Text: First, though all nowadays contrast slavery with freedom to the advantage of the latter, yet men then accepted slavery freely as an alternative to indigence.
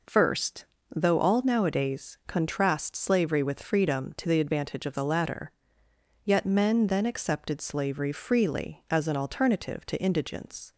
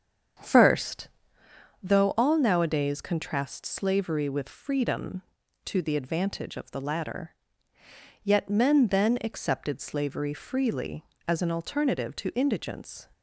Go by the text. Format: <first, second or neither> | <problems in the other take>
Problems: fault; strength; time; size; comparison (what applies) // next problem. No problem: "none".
first | starts louder than the rest; strong; until 2.1 s; 7.5 dB